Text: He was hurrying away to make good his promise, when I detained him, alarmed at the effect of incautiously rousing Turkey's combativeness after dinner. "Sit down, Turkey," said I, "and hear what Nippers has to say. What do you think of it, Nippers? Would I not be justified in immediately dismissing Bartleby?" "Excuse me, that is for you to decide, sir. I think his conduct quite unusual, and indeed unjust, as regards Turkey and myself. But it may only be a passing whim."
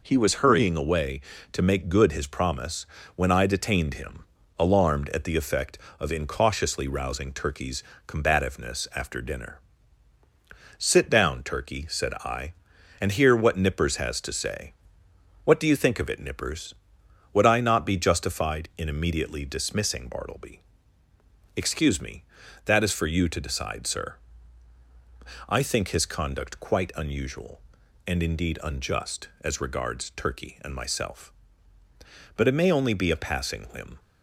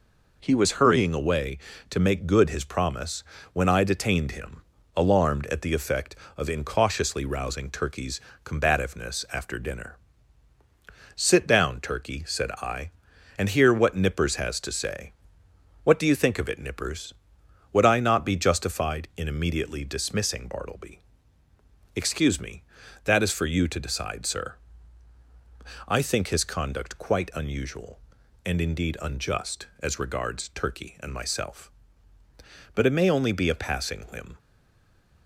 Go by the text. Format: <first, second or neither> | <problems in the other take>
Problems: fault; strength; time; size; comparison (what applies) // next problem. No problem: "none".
first | pauses between "Turkey's" and "combativeness"; slight; at 8.1 s; 0.24 s long; slight in the first // stays silent after the last word; slight; from 34.3 s on; 0.9 s long